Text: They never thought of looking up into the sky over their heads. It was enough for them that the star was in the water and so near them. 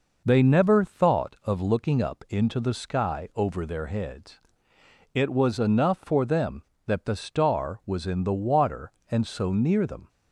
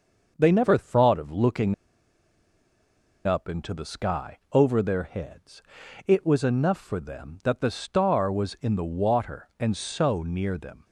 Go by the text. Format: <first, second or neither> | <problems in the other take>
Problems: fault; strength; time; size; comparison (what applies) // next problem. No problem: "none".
first | starts louder than the rest; noticeable; until 1.3 s; 6 dB // pauses between "looking" and "up"; strong; at 1.7 s; 1.5 s long